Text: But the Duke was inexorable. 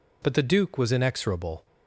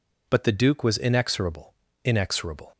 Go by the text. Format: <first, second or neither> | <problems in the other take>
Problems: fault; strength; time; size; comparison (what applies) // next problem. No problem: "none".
first | says "inexorable" twice; at 2.0 s